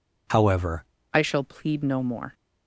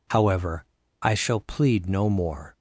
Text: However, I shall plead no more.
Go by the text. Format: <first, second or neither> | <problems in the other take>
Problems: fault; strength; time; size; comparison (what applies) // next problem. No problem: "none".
second | changes voice at "I"; from 1.1 s on; 1.2 s long